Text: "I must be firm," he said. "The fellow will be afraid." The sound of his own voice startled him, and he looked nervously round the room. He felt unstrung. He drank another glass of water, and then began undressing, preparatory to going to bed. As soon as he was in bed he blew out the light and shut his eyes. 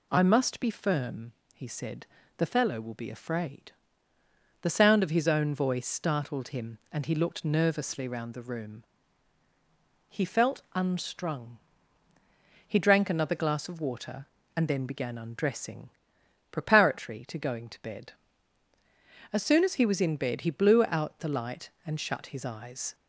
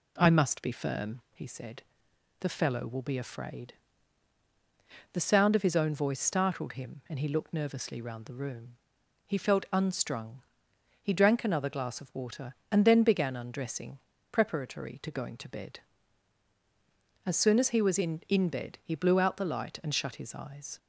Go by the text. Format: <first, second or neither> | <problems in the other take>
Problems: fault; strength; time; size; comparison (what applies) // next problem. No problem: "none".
first | says "in" twice; at 18.2 s